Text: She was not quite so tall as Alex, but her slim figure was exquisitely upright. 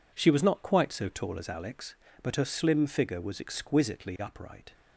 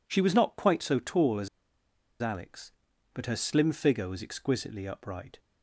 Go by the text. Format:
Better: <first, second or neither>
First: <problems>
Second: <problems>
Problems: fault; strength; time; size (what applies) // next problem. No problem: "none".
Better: first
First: none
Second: pauses between "as" and "Alex"; noticeable; at 1.4 s; 0.73 s long